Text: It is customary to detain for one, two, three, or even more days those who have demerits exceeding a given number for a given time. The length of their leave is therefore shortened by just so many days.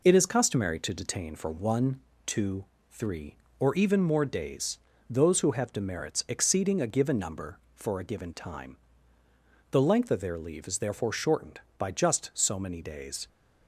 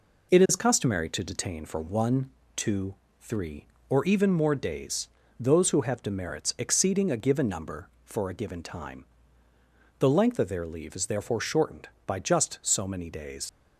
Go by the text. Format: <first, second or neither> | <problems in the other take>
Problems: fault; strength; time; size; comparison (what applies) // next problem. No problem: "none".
first | pauses between "days" and "those"; slight; at 5.0 s; 0.30 s long; slight in the first // leaves "days" unfinished; at 13.4 s; 70 ms